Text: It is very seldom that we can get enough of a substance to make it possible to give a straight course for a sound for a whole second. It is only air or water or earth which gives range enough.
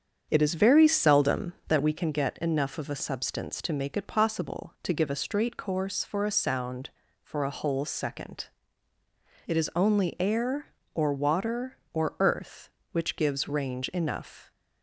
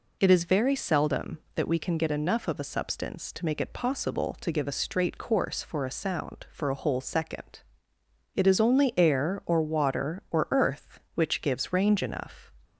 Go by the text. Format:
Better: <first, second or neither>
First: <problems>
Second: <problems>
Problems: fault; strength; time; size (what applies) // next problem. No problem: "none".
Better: second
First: starts louder than the rest; strong; until 1.8 s; 7.5 dB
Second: none